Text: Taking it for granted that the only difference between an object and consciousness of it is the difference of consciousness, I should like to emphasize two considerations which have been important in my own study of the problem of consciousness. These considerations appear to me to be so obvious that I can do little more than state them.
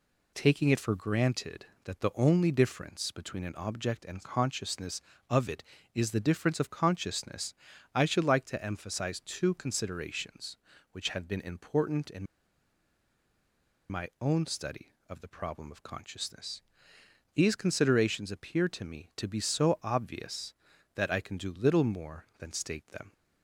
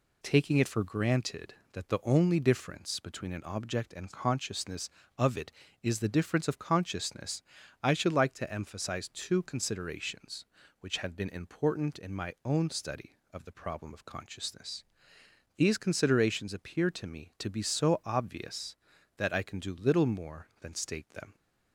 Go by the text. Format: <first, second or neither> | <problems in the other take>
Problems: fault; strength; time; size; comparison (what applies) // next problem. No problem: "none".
second | pauses between "in" and "my"; strong; at 12.2 s; 1.6 s long